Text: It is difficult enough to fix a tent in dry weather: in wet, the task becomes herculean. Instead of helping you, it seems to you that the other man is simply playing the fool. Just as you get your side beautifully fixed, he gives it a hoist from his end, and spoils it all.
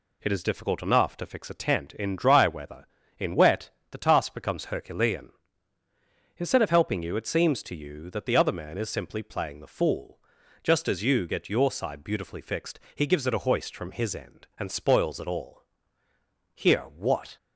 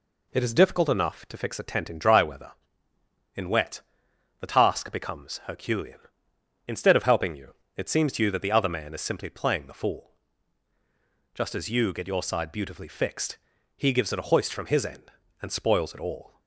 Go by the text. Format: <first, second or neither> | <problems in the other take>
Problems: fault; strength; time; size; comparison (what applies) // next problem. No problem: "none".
second | goes on to say "Here what"; noticeable; from 16.5 s on; 0.82 s long